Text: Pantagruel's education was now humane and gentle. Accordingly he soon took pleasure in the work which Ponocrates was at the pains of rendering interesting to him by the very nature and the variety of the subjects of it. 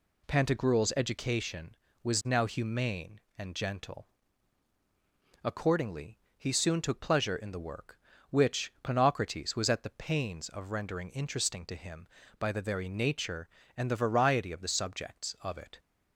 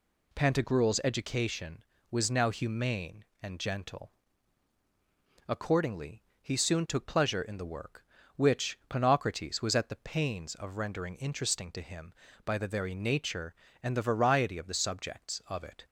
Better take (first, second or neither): neither